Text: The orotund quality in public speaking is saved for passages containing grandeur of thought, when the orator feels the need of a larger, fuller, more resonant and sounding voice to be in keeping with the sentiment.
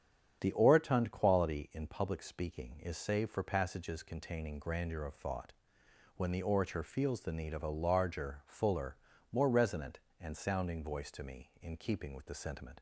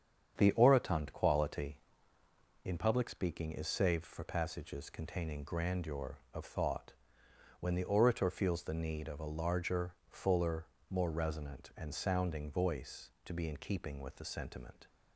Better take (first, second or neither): second